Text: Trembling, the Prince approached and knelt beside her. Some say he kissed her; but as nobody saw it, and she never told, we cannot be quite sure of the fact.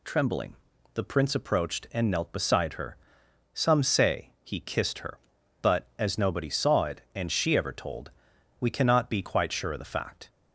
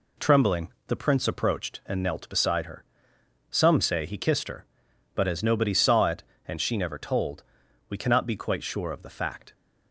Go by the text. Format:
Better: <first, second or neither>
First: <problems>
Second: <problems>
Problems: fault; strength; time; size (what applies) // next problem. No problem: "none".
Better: second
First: says "ever" for "never"; at 7.5 s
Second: none